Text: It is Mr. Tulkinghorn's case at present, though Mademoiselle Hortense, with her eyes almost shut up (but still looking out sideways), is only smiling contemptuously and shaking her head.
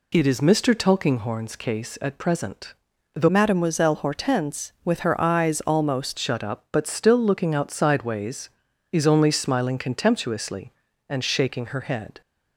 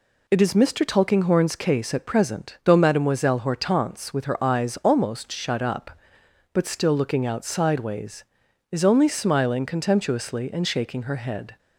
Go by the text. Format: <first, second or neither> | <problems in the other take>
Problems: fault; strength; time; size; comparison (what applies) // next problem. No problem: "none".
second | changes voice from "Mademoiselle" to "almost"; from 3.2 to 6.1 s; 2.9 s long